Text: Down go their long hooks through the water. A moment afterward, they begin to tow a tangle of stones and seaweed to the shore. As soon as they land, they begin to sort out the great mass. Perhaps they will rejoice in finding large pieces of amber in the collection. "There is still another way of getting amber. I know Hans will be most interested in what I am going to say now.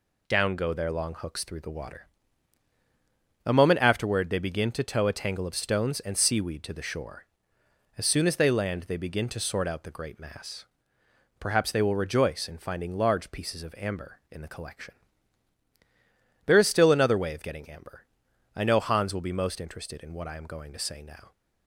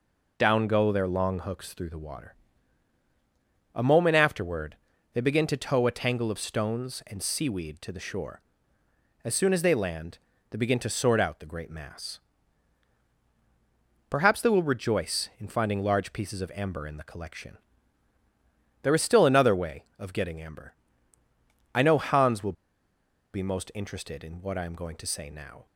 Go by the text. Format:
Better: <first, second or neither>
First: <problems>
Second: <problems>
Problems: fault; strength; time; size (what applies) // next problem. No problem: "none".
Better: first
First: none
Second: pauses between "will" and "be"; noticeable; at 22.5 s; 0.80 s long